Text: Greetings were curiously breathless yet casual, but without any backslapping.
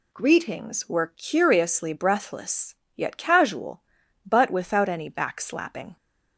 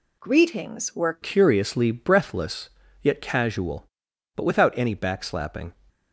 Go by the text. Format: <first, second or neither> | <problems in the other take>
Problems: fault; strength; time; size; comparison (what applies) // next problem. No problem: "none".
first | changes voice at "curiously"; from 1.2 s on; 4.5 s long // pauses between "breathless" and "yet"; slight; at 2.7 s; 0.32 s long; slight in the first